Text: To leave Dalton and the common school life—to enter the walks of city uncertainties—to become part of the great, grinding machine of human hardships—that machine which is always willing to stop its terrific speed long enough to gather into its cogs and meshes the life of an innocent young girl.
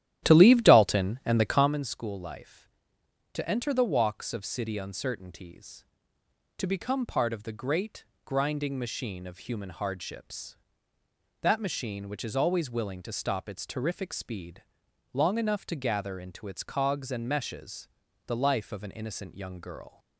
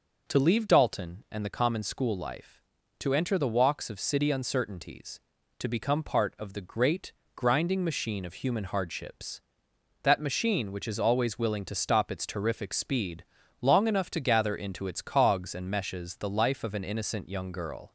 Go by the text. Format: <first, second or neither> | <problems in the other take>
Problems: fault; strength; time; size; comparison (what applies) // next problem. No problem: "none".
second | starts louder than the rest; strong; until 1.7 s; 12 dB // pauses between "speed" and "long"; noticeable; at 14.6 s; 0.50 s long; slight in the second // pauses between "meshes" and "the"; at 17.8 s; 0.38 s long